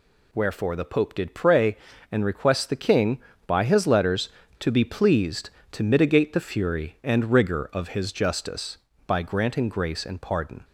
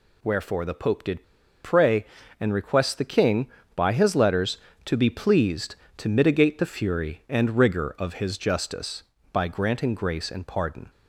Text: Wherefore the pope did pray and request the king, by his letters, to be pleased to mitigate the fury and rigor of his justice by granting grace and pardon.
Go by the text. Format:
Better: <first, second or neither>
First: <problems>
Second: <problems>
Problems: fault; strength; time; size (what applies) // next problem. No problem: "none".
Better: first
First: none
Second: pauses between "did" and "pray"; at 1.2 s; 0.41 s long